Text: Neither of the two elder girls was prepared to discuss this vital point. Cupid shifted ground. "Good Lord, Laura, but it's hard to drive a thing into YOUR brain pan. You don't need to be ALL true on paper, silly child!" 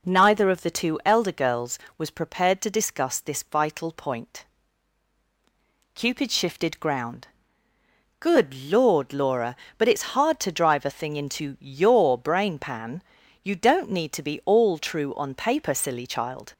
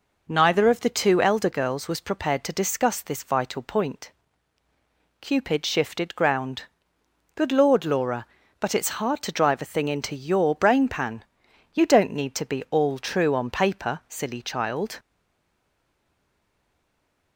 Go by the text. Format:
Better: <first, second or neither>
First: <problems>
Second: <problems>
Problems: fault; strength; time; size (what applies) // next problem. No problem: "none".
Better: first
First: none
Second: stays silent after the last word; from 14.9 s on; 2.4 s long